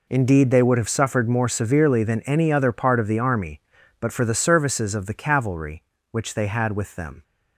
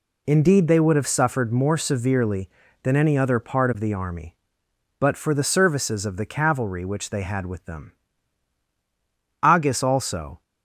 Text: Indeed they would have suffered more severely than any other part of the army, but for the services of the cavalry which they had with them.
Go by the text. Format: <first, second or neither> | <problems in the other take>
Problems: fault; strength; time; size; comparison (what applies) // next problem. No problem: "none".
first | goes on to say "Agis also"; noticeable; from 9.4 s on; 1.0 s long